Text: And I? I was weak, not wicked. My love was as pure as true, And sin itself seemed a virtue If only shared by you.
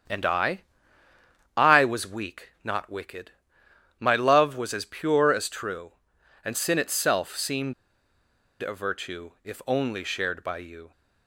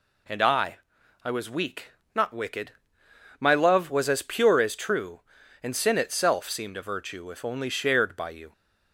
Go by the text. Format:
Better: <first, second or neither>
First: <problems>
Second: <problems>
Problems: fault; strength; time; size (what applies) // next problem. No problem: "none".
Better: second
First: starts louder than the rest; strong; until 2.0 s; 8 dB // pauses between "seemed" and "a"; noticeable; at 7.7 s; 0.89 s long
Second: none